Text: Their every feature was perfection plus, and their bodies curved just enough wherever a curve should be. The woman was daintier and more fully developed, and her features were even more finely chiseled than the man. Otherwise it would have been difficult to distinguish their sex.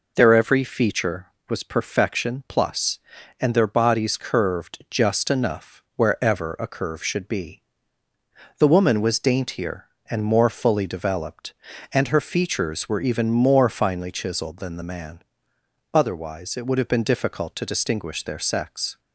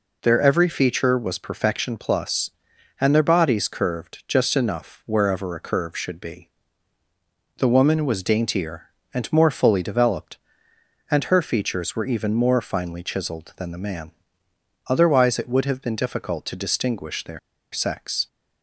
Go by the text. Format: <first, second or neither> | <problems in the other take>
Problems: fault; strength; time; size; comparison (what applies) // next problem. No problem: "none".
first | pauses between "their" and "sex"; slight; at 17.3 s; 0.33 s long